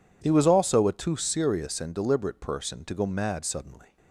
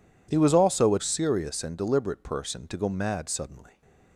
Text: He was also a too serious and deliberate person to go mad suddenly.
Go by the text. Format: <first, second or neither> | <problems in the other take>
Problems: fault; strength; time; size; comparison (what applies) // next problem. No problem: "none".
first | skips "too"; at 0.9 s